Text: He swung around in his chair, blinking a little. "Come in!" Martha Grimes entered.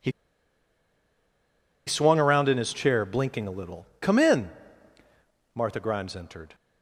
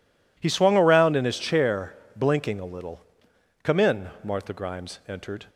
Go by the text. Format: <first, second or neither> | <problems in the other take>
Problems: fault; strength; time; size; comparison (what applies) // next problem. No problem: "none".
second | pauses between "He" and "swung"; strong; at 0.1 s; 1.7 s long